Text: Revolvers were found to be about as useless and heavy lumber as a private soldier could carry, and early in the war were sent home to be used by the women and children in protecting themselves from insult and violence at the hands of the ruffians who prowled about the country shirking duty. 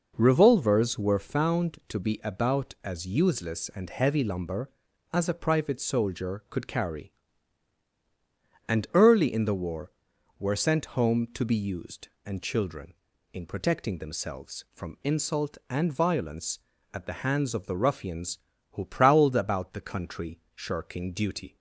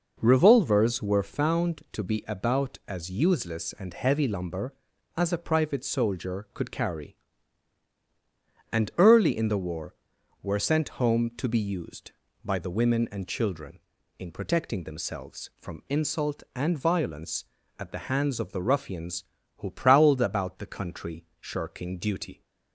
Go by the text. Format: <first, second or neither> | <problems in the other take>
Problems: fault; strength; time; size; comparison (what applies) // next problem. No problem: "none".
second | skips "by the women"; at 12.1 s // pauses between "country" and "shirking"; slight; at 20.4 s; 0.16 s long; slight in the second